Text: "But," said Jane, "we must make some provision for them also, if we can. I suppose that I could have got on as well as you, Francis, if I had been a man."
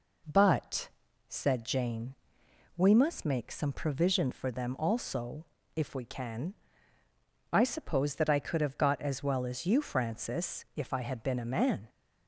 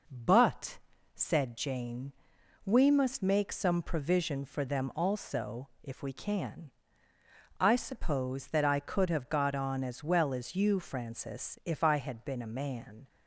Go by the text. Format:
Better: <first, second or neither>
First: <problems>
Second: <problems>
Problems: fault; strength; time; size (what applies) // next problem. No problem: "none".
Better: second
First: skips "on"; at 9.0 s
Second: none